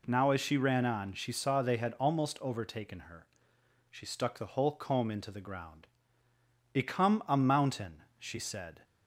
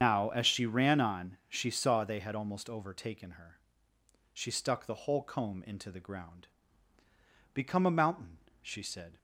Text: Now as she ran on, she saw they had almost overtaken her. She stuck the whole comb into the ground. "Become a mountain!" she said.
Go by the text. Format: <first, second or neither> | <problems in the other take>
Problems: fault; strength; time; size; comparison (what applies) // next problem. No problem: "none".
first | loses the start of "Now"; at 0.0 s; 75 ms // starts louder than the rest; strong; until 1.0 s; 7.5 dB